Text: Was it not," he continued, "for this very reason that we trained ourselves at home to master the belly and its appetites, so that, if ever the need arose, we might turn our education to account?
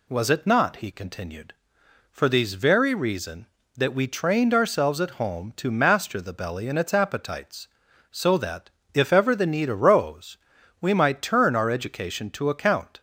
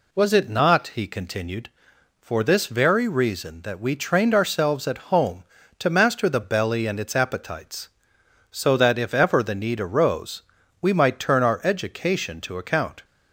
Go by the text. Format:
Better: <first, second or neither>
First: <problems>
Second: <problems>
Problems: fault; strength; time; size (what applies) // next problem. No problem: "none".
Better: second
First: says "these" for "this"; at 2.3 s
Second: none